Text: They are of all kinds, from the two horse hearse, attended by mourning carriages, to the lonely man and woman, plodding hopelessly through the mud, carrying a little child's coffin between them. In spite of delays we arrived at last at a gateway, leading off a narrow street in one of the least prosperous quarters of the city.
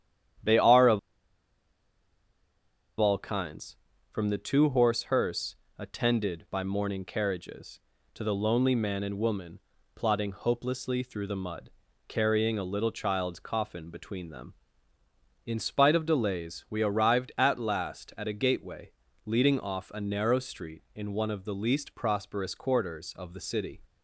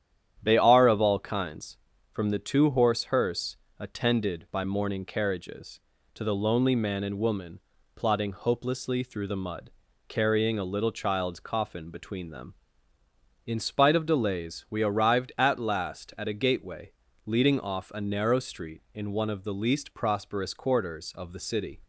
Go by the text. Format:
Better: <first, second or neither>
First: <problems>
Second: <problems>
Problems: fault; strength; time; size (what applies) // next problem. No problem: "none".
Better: second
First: starts louder than the rest; strong; until 3.4 s; 10 dB // pauses between "of" and "all"; strong; at 0.9 s; 1.9 s long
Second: starts louder than the rest; strong; until 1.4 s; 10 dB